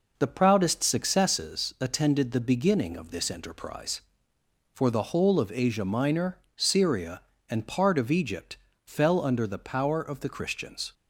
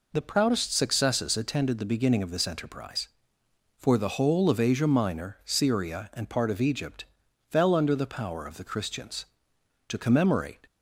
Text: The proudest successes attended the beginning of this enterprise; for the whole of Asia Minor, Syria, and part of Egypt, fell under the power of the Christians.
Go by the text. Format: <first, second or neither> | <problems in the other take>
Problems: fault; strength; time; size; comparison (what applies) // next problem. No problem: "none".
first | goes on to say "To commemorate"; noticeable; from 9.8 s on; 0.72 s long